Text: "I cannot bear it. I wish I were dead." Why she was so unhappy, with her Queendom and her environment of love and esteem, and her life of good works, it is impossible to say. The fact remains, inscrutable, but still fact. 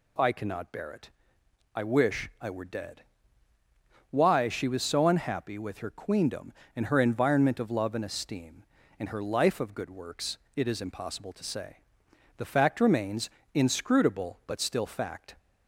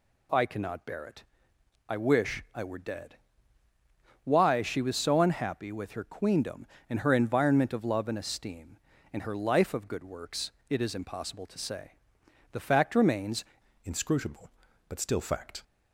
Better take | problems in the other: first | changes voice at "inscrutable"; from 13.8 s on; 1.8 s long

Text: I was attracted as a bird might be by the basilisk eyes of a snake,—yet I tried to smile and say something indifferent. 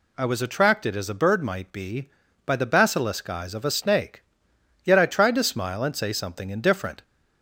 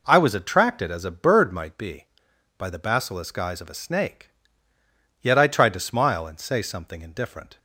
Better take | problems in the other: neither | none

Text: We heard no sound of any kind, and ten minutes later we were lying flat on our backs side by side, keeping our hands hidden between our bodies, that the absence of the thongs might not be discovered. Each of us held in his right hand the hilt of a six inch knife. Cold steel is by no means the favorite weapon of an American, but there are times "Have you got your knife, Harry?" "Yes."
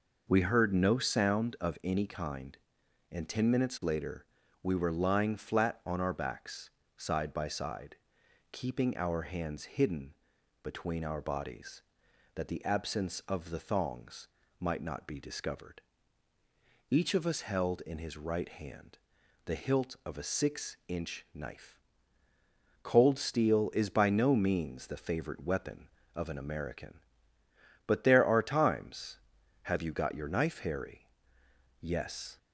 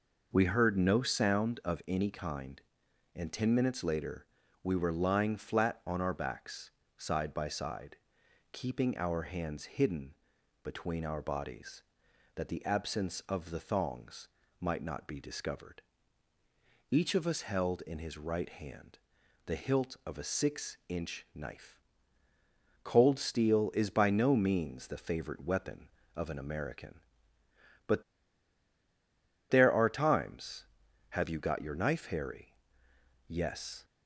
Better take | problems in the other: first | pauses between "later" and "we"; at 4.2 s; 0.40 s long; also in the first // pauses between "backs" and "side"; slight; at 6.6 s; 0.26 s long; slight in the first // pauses between "hidden" and "between"; noticeable; at 10.1 s; 0.50 s long; noticeable in the first // pauses between "thongs" and "might"; slight; at 14.2 s; 0.30 s long; slight in the first // pauses between "hand" and "the"; at 18.9 s; 0.44 s long; also in the first // pauses between "but" and "there"; strong; at 28.0 s; 1.4 s long

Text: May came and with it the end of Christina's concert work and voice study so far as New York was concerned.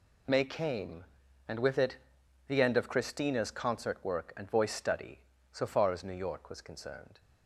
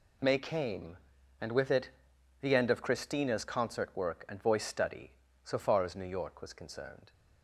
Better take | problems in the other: neither | pauses between "it" and "the"; noticeable; the same in both

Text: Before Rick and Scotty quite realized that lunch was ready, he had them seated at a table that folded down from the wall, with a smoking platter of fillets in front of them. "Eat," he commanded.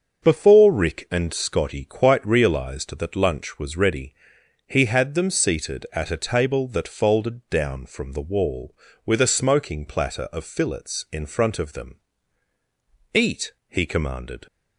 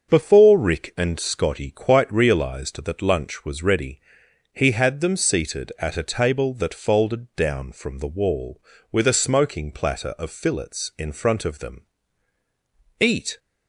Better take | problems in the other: first | starts louder than the rest; until 1.1 s; 6.5 dB; also in the first // stops before "he commanded"; at 13.3 s

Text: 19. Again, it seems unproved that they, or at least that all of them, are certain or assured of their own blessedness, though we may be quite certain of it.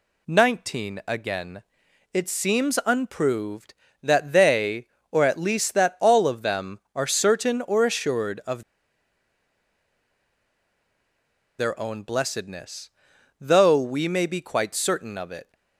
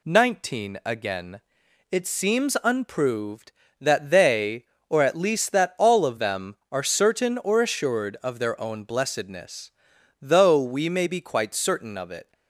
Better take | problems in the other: second | pauses between "of" and "their"; strong; at 8.6 s; 2.9 s long

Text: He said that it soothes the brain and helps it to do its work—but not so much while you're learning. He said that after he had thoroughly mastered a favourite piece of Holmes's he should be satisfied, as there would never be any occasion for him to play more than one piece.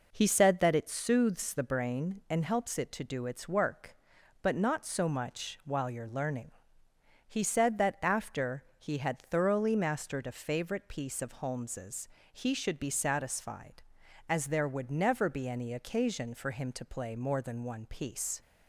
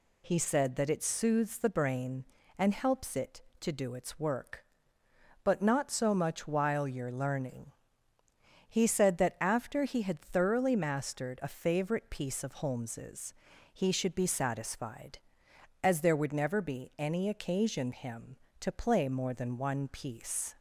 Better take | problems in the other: first | pauses between "Holmes's" and "he"; slight; at 13.3 s; 0.36 s long; slight in the first // skips "for"; at 17.9 s

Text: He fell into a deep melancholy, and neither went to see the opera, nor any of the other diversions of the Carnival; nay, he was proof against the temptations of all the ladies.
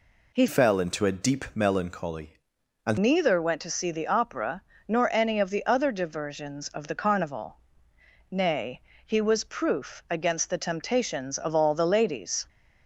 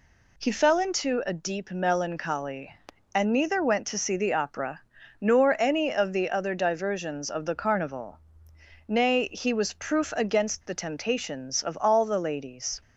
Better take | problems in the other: second | changes voice from "fell" to "and"; from 0.4 to 2.9 s; 2.5 s long

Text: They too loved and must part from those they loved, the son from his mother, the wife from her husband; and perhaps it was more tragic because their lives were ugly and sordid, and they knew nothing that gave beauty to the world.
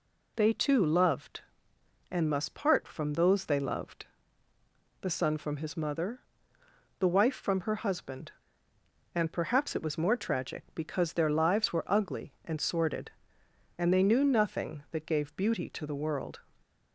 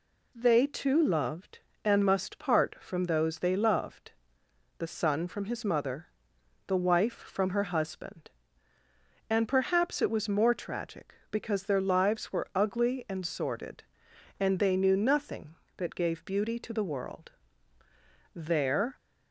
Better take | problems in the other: first | goes on to say "There"; noticeable; from 18.3 s on; 0.62 s long

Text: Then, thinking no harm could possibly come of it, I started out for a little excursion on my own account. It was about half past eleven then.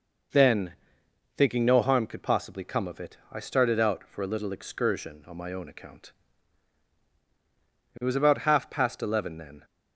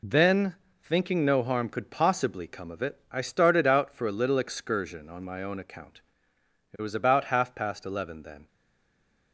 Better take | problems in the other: first | stays silent after the last word; slight; from 8.4 s on; 0.9 s long

